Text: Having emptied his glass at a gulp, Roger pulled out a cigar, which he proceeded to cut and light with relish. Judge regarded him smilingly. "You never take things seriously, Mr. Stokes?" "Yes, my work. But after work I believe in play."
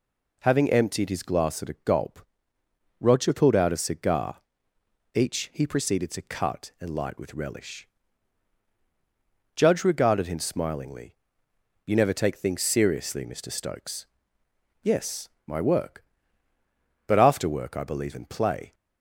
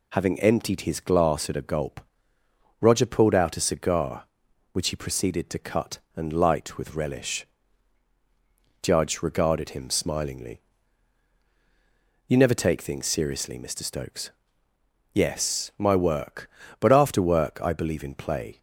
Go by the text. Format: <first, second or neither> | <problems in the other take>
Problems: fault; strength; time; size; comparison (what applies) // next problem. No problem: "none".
second | says "each" for "which"; at 5.1 s